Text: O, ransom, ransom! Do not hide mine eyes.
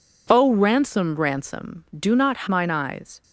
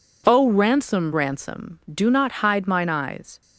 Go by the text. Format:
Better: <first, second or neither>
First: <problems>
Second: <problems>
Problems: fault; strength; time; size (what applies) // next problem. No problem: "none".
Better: second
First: skips "hide"; at 2.4 s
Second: none